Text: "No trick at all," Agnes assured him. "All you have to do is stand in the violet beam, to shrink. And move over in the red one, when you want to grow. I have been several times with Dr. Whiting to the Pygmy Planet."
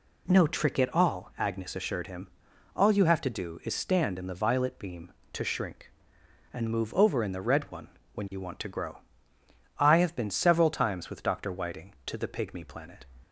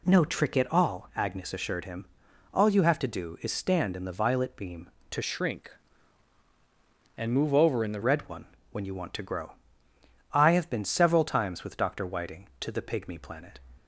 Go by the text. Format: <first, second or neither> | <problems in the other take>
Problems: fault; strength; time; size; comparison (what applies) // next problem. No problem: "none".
first | changes voice from "shrink" to "the"; from 5.2 to 8.0 s; 2.8 s long